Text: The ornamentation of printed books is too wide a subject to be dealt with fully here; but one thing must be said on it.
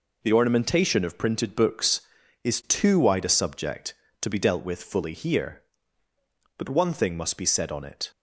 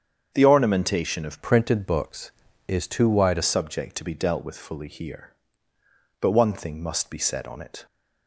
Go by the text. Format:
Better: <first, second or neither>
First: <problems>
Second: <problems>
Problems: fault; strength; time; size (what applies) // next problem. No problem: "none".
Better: first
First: none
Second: starts louder than the rest; strong; until 1.3 s; 7 dB // changes voice from "printed" to "a"; from 1.4 to 3.4 s; 2.0 s long